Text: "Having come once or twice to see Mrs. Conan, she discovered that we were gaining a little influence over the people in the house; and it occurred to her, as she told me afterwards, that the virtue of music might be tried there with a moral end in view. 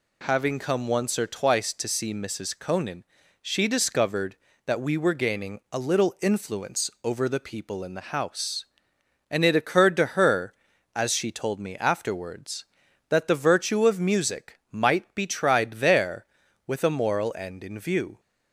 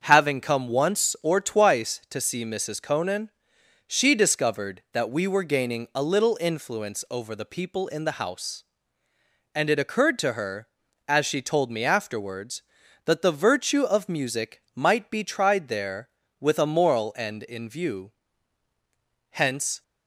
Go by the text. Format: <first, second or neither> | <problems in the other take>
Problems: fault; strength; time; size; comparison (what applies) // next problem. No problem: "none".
first | starts louder than the rest; until 1.0 s; 7 dB // goes on to say "Hence"; from 19.3 s on; 0.52 s long